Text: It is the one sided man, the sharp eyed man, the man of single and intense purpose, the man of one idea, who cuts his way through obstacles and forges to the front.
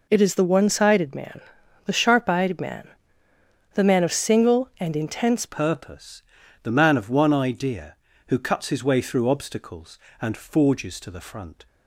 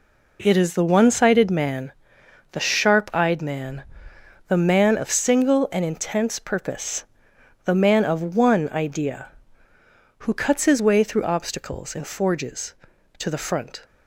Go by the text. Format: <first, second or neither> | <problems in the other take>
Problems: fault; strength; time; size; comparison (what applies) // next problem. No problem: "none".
second | changes voice at "purpose"; from 5.4 s on; 6.2 s long